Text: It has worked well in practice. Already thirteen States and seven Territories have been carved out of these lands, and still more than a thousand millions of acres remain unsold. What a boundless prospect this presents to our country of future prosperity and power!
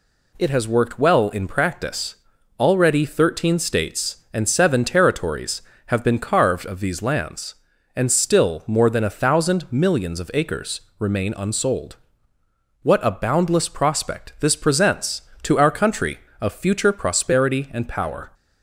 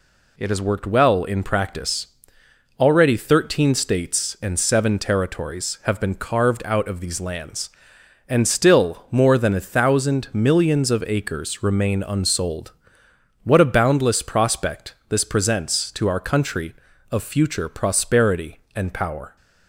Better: second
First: skips "out"; at 6.6 s // pauses between "acres" and "remain"; slight; at 10.7 s; 0.18 s long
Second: none

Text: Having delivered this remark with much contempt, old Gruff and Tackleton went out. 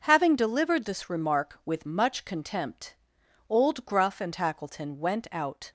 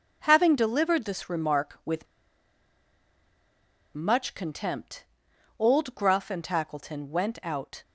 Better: first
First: none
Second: pauses between "with" and "much"; strong; at 2.0 s; 1.9 s long

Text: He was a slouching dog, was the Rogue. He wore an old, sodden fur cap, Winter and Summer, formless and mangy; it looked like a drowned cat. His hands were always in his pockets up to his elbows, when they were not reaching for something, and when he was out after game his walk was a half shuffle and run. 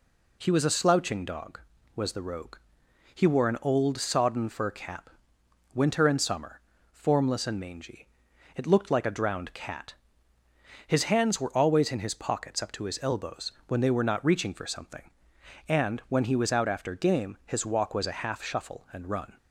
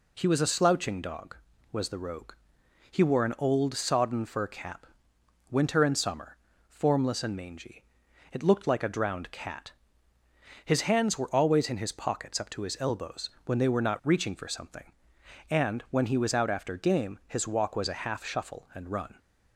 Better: neither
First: none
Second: none

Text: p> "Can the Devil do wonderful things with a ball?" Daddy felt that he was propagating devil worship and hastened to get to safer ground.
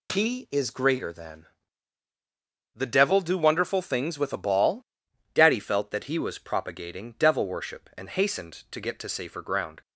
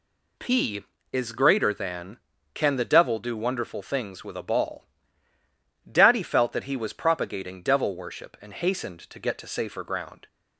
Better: second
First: skips "Can"; at 2.0 s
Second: none

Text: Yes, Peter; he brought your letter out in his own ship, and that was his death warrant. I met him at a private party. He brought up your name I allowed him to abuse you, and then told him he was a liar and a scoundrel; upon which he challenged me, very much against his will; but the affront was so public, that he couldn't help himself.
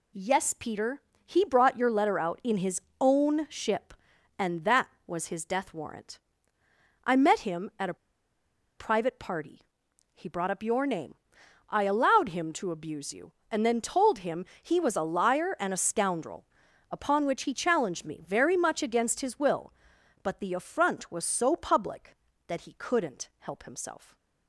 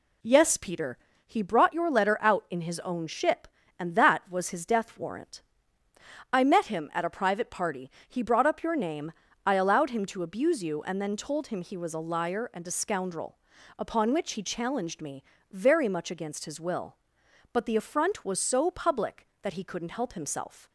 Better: second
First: pauses between "his" and "own"; slight; at 2.7 s; 0.22 s long // pauses between "a" and "private"; noticeable; at 7.9 s; 0.82 s long // pauses between "name" and "I"; noticeable; at 11.1 s; 0.52 s long // pauses between "him" and "he"; slight; at 14.4 s; 0.16 s long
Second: pauses between "name" and "I"; slight; at 9.1 s; 0.32 s long

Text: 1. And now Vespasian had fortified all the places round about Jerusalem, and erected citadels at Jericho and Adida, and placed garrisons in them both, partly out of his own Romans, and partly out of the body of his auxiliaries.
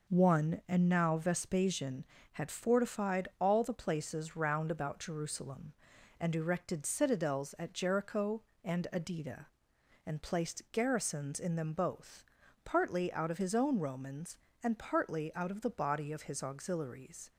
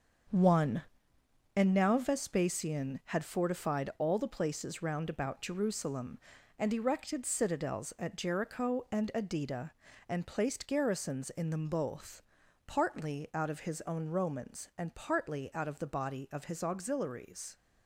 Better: first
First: none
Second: gets quieter; strong; throughout; 7.5 dB

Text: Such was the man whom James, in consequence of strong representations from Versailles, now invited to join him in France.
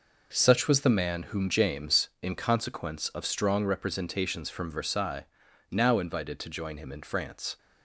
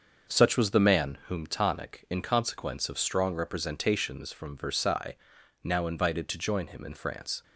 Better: first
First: none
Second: starts louder than the rest; until 1.4 s; 6.5 dB // says "Tonic" for "James"; at 1.4 s

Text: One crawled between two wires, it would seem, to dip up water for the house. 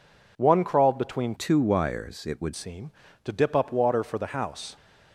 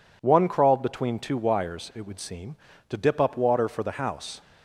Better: second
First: changes voice from "two" to "would"; from 1.3 to 2.5 s; 1.2 s long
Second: none

